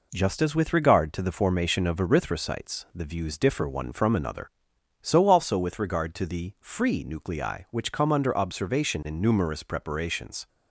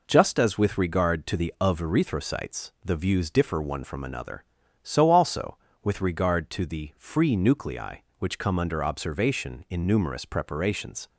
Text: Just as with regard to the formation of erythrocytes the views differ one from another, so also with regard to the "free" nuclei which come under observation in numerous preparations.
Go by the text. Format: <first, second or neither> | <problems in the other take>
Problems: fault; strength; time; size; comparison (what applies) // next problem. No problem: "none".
first | skips "formation"; at 1.5 s